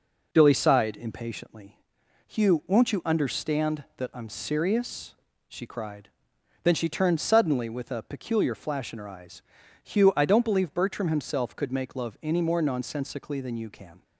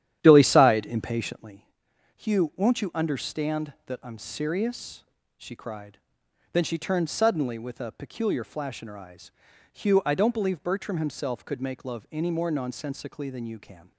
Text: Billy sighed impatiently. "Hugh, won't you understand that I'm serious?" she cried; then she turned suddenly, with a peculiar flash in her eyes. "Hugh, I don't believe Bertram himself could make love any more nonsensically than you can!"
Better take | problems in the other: first | starts louder than the rest; strong; until 1.6 s; 11 dB

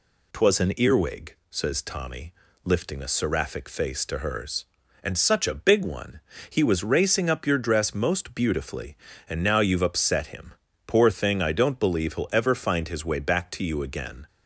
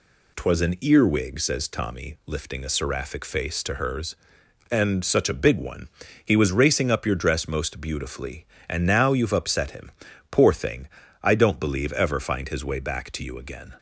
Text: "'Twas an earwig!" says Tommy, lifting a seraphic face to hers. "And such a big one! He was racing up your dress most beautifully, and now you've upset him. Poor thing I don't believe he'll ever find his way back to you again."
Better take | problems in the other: first | pauses between "thing" and "I"; slight; at 10.8 s; 0.34 s long // skips "he'll"; at 11.9 s

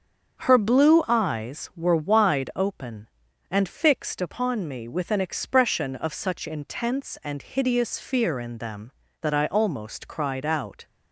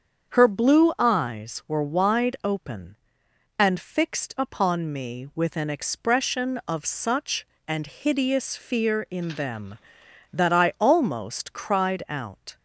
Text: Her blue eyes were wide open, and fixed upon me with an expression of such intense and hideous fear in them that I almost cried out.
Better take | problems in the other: first | starts louder than the rest; strong; until 1.3 s; 7.5 dB; strong in the first // skips "intense"; at 7.5 s

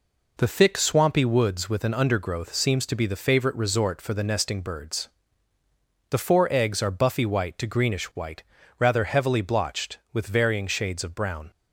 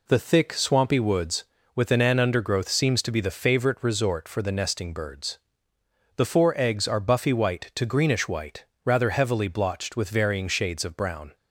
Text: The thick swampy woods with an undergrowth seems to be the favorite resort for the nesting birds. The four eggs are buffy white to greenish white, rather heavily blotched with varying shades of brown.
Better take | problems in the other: first | says "an" twice; at 1.9 s

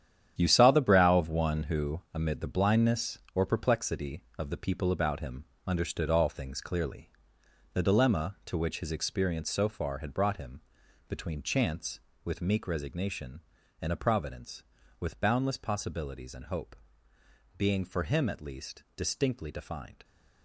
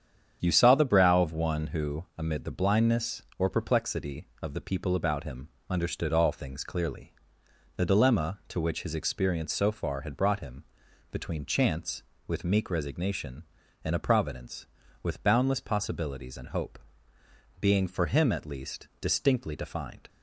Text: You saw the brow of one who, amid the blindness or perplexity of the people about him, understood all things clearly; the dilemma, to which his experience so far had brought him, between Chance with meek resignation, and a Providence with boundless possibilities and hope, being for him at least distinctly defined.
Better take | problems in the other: second | gets quieter; strong; throughout; 10.5 dB // starts louder than the rest; strong; until 1.4 s; 9.5 dB; strong in the second

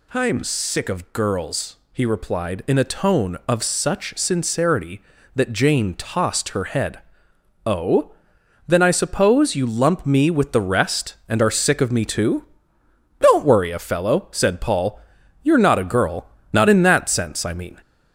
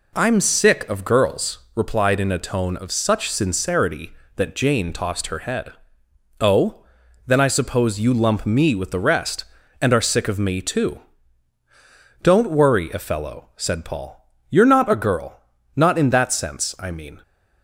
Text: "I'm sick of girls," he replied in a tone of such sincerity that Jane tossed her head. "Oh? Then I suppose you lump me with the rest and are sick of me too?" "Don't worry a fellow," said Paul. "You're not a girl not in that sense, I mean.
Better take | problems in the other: first | skips "he"; at 1.6 s // pauses between "girl" and "not"; slight; at 15.3 s; 0.36 s long; slight in the first

